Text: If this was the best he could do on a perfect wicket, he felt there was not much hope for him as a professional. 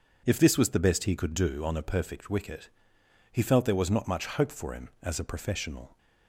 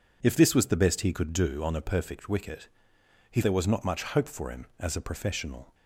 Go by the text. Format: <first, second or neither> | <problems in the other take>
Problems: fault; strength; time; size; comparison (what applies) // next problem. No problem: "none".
first | skips "felt"; at 3.4 s